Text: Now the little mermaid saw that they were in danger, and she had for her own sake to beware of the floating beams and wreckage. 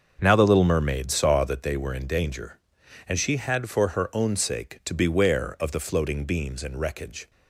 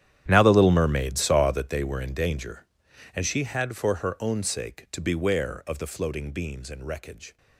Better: first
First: starts louder than the rest; until 1.2 s; 6.5 dB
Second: gets quieter; strong; throughout; 17.5 dB // starts louder than the rest; strong; until 1.2 s; 10.5 dB

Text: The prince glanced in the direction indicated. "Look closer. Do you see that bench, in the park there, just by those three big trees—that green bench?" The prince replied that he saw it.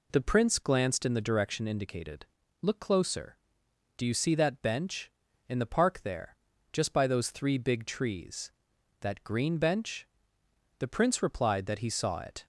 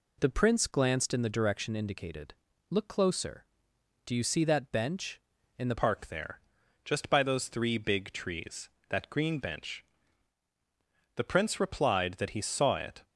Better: first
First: none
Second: changes voice at "park"; from 5.7 s on; 7.3 s long

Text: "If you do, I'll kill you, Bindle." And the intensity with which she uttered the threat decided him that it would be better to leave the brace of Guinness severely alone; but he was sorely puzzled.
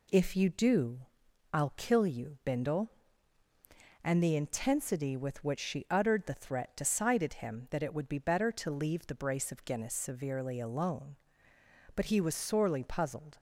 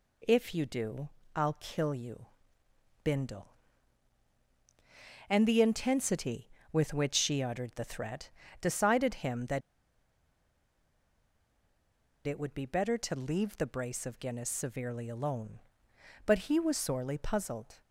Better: first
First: none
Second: pauses between "threat" and "decided"; slight; at 8.3 s; 0.30 s long // pauses between "that" and "it"; strong; at 9.6 s; 2.6 s long

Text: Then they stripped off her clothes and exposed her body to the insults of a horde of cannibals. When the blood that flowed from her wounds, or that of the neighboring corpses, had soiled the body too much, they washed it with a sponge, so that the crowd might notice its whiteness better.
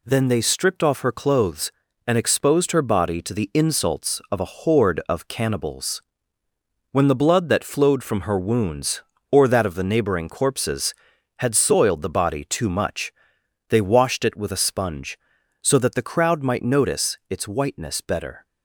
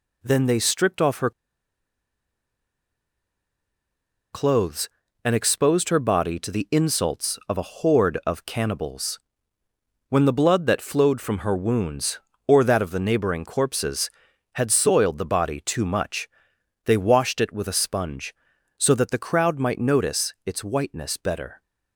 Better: first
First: none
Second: pauses between "her" and "clothes"; strong; at 1.3 s; 3.0 s long

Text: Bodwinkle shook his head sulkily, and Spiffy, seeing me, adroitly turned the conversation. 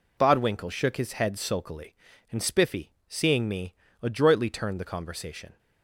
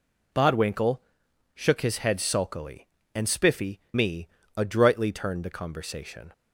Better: first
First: none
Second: pauses between "Bodwinkle" and "shook"; noticeable; at 0.9 s; 0.56 s long // skips "seeing"; at 3.8 s

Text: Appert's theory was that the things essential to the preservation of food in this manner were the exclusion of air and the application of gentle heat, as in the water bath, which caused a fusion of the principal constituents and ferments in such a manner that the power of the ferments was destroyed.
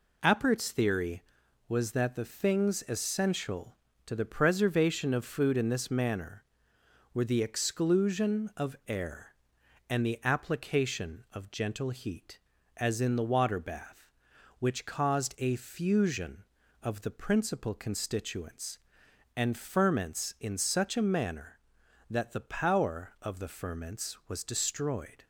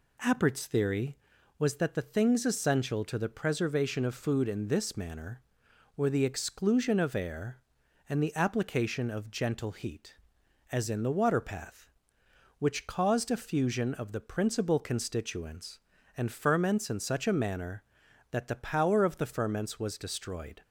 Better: first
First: none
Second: says "path" for "bath"; at 11.3 s

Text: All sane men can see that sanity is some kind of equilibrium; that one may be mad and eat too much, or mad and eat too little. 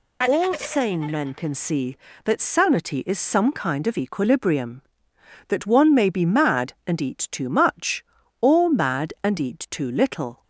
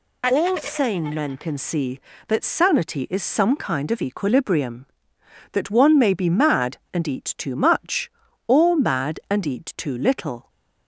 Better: neither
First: none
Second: none

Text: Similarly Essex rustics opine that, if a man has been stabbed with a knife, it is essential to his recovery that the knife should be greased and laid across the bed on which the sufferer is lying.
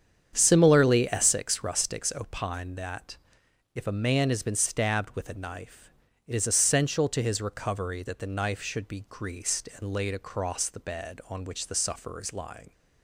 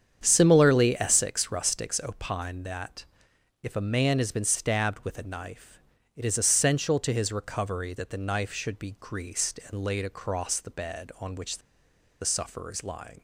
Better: first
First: starts louder than the rest; strong; until 1.3 s; 8 dB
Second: starts louder than the rest; strong; until 1.2 s; 8 dB // pauses between "which" and "the"; noticeable; at 11.5 s; 0.62 s long

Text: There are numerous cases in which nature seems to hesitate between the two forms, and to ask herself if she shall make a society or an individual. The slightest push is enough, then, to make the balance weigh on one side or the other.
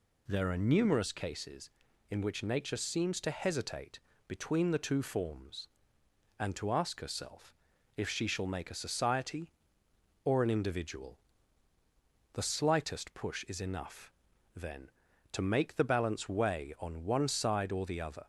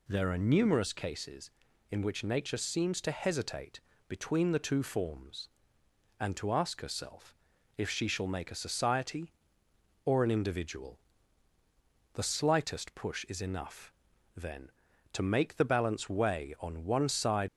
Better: first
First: pauses between "hesitate" and "between"; slight; at 4.0 s; 0.26 s long // pauses between "herself" and "if"; at 7.5 s; 0.42 s long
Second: pauses between "hesitate" and "between"; slight; at 3.8 s; 0.26 s long // pauses between "herself" and "if"; at 7.3 s; 0.42 s long // stops before "or the other"; at 17.4 s

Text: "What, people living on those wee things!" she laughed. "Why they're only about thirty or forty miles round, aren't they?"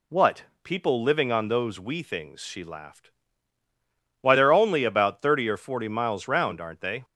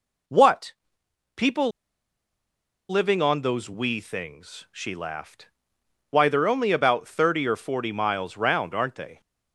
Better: first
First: none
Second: pauses between "people" and "living"; at 1.7 s; 1.1 s long

